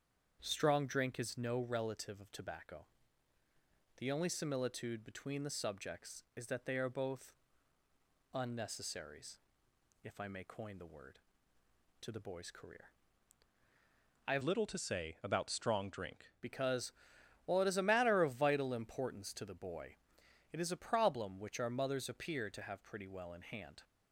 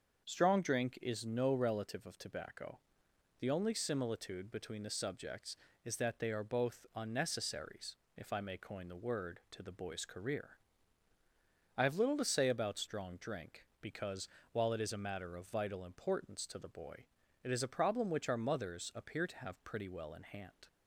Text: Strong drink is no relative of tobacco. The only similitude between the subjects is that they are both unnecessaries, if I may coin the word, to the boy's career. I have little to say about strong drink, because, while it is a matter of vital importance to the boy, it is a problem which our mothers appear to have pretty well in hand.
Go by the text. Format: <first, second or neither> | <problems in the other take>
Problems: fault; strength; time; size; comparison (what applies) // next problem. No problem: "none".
second | starts louder than the rest; strong; until 1.4 s; 7.5 dB; also in the second // pauses between "both" and "unnecessaries"; noticeable; at 7.3 s; 0.98 s long // changes voice from "little" to "drink"; from 14.4 to 16.2 s; 1.8 s long